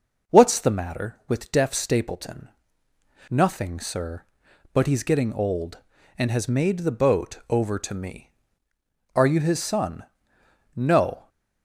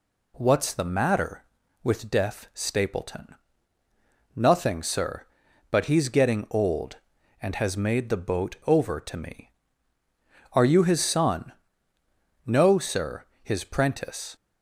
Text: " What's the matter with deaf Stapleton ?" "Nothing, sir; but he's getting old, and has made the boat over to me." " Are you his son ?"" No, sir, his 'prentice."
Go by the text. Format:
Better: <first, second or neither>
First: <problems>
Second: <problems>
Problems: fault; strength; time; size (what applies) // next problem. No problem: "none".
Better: second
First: starts louder than the rest; until 1.3 s; 7 dB // stops before "sir his prentice"; at 11.2 s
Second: none